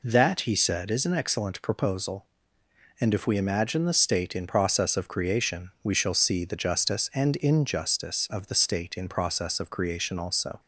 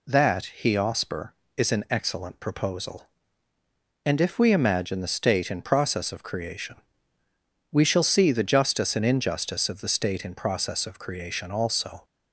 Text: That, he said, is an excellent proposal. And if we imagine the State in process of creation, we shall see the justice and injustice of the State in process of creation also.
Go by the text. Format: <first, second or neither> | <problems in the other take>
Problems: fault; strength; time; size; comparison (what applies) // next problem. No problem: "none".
first | says "osper" for "said"; at 0.7 s